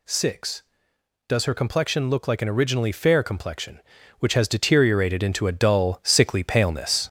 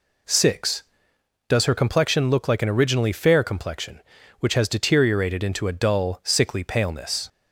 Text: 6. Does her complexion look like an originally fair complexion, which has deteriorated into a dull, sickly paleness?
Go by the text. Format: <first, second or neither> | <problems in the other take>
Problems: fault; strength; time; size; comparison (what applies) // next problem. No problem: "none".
second | gets louder; noticeable; throughout; 5.5 dB